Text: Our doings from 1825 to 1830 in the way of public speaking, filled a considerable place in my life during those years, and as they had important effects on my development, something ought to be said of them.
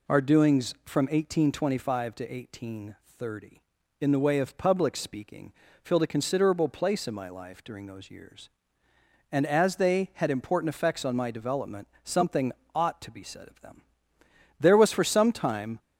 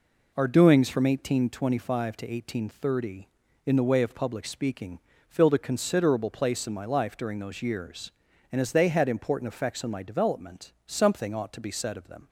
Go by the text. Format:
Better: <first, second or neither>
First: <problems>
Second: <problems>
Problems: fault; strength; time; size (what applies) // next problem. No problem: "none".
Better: second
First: pauses between "something" and "ought"; slight; at 12.5 s; 0.22 s long // goes on to say "There was for some time"; noticeable; from 14.6 s on; 1.1 s long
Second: none